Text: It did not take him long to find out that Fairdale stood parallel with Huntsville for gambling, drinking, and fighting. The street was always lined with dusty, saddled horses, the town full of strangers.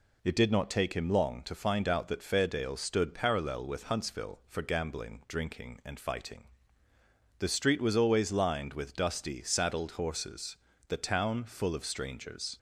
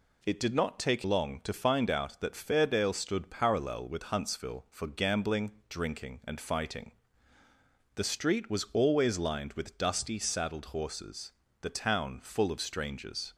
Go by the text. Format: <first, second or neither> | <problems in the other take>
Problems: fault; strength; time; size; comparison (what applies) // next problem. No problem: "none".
first | skips "him"; at 1.0 s